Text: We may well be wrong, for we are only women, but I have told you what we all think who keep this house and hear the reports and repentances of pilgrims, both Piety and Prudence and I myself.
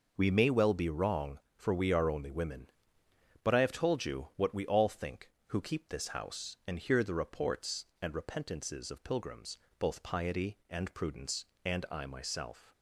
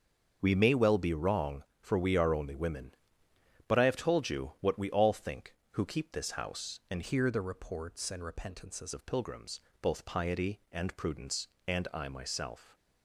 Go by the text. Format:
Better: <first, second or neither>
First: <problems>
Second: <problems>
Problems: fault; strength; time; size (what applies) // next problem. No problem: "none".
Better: first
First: none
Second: starts louder than the rest; until 1.4 s; 6.5 dB // changes voice from "hear" to "repentances"; from 7.0 to 8.9 s; 1.9 s long